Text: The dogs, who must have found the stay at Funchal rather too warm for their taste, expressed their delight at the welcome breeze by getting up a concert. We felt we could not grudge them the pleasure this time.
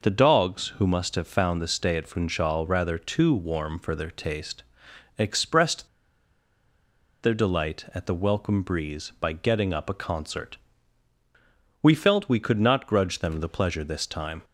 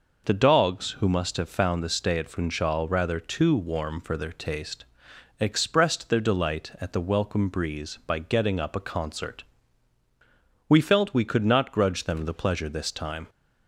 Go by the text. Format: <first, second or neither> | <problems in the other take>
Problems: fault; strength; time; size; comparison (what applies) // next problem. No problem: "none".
second | pauses between "expressed" and "their"; strong; at 5.8 s; 1.3 s long